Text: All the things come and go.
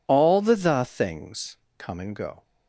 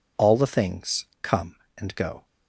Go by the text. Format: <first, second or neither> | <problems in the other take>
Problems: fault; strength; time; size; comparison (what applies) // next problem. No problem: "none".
second | says "the" twice; at 0.5 s // pauses between "things" and "come"; slight; at 1.5 s; 0.22 s long; slight in the second